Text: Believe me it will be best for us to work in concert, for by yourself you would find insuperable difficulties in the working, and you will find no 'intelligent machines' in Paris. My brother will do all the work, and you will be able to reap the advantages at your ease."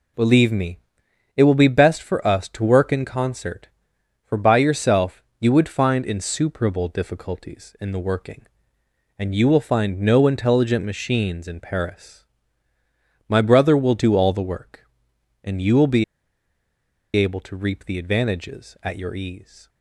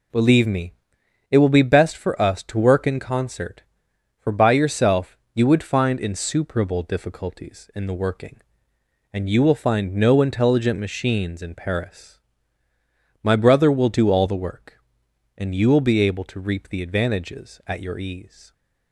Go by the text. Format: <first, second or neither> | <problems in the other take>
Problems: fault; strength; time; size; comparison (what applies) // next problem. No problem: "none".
second | pauses between "me" and "it"; noticeable; at 0.7 s; 0.58 s long; noticeable in the second // pauses between "yourself" and "you"; slight; at 5.2 s; 0.20 s long; slight in the second // pauses between "be" and "able"; at 16.0 s; 1.1 s long